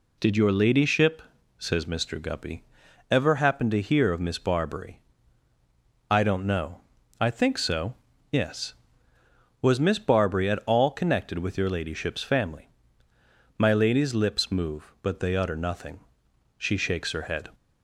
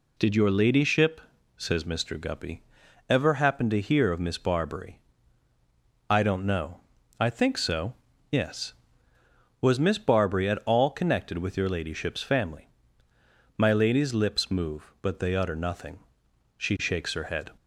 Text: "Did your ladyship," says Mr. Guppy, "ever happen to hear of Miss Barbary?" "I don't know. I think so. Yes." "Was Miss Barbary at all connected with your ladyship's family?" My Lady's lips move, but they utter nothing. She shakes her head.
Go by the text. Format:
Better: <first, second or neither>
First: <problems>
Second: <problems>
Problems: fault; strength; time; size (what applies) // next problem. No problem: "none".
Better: neither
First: none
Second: none